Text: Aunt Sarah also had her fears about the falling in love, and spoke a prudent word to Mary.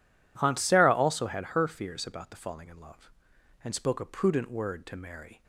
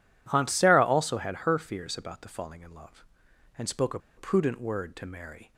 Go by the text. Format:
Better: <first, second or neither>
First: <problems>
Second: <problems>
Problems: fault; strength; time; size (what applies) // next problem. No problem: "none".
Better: first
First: none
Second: pauses between "a" and "prudent"; slight; at 3.9 s; 0.17 s long